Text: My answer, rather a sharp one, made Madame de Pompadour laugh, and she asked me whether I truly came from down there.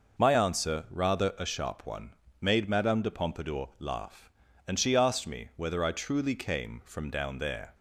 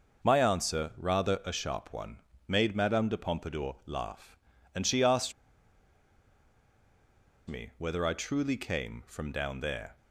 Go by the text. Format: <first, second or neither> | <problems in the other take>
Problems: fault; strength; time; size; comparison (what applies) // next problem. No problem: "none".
first | pauses between "asked" and "me"; strong; at 5.3 s; 2.1 s long